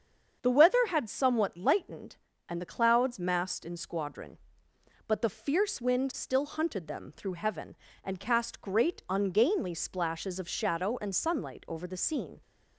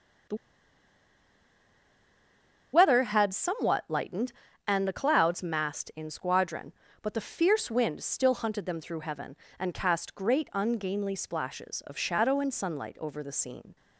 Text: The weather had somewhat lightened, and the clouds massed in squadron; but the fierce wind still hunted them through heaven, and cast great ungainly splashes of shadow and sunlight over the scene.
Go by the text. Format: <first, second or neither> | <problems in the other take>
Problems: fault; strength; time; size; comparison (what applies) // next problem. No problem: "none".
first | starts louder than the rest; until 3.6 s; 6.5 dB; strong in the first // pauses between "The" and "weather"; strong; at 0.3 s; 2.3 s long